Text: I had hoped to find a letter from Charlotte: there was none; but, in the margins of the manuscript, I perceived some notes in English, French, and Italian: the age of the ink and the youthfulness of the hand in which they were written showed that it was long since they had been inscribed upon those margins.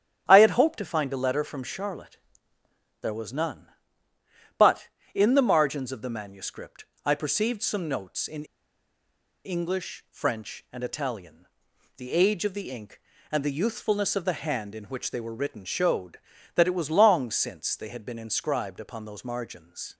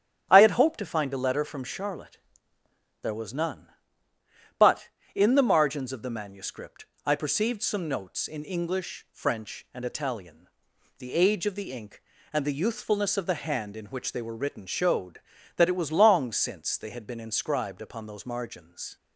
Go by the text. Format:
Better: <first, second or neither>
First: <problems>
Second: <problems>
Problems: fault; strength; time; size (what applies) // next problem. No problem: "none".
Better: second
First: starts louder than the rest; strong; until 1.2 s; 9.5 dB // pauses between "in" and "English"; at 8.4 s; 0.99 s long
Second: starts louder than the rest; strong; until 1.3 s; 9.5 dB